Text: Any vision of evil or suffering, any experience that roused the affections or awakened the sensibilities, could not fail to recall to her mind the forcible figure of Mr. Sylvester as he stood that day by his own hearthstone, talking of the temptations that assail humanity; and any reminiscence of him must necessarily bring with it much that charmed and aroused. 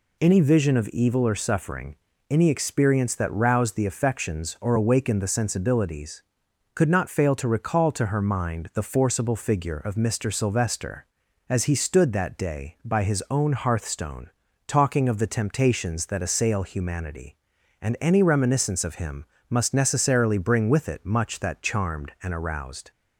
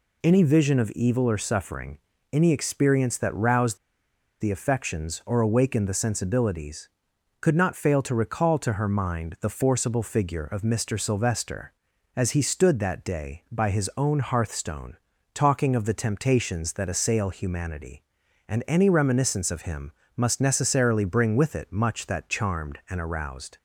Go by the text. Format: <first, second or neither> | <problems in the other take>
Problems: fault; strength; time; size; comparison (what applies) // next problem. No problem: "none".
first | pauses between "roused" and "the"; noticeable; at 3.7 s; 0.63 s long // pauses between "him" and "must"; slight; at 19.9 s; 0.24 s long; slight in the first